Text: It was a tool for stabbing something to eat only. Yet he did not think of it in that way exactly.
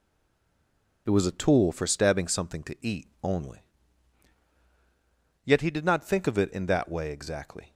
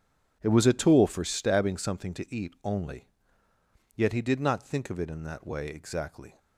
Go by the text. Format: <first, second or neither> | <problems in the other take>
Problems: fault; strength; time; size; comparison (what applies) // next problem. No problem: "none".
second | stays silent before the first word; until 1.0 s; 1.0 s long